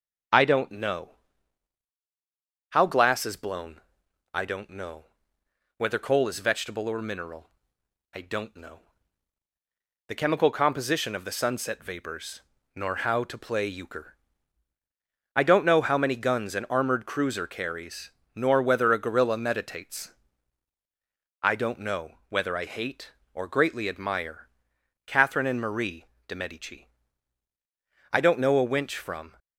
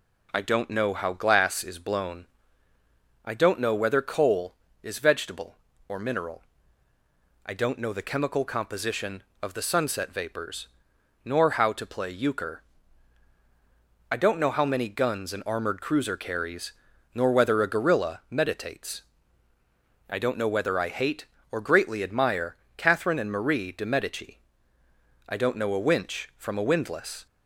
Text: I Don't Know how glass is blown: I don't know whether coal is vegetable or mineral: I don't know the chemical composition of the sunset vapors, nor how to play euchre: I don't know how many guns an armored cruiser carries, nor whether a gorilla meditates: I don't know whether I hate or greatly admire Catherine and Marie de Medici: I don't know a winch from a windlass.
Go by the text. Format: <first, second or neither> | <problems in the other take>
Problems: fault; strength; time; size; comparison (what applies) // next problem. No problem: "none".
second | starts louder than the rest; until 2.9 s; 7 dB // pauses between "Know" and "how"; strong; at 1.1 s; 1.6 s long // pauses between "know" and "whether"; noticeable; at 5.0 s; 0.74 s long // pauses between "know" and "the"; strong; at 8.8 s; 1.2 s long // pauses between "admire" and "Catherine"; noticeable; at 24.4 s; 0.58 s long; slight in the second // pauses between "Marie" and "de"; slight; at 26.0 s; 0.22 s long // stops before "a windlass"; at 29.3 s